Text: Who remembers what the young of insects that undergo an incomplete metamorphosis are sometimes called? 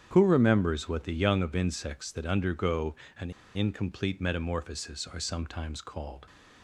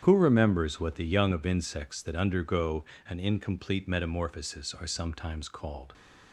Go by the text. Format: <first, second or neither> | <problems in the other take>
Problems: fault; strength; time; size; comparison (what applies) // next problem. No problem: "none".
second | starts louder than the rest; strong; until 1.1 s; 9 dB; strong in the second // pauses between "undergo" and "an"; slight; at 2.9 s; 0.22 s long; slight in the second // pauses between "an" and "incomplete"; slight; at 3.2 s; 0.25 s long